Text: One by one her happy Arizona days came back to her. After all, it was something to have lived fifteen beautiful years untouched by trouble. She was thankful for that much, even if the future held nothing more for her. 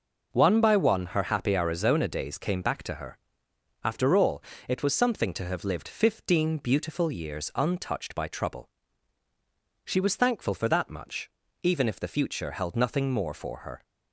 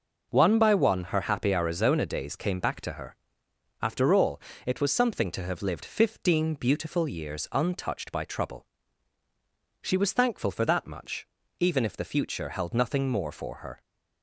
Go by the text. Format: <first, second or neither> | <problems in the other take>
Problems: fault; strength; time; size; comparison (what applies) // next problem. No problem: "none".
neither | none